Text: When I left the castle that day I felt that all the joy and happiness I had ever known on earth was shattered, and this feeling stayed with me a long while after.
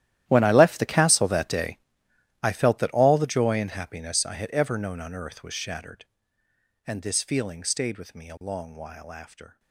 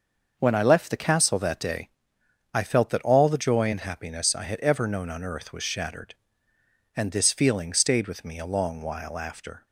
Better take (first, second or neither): second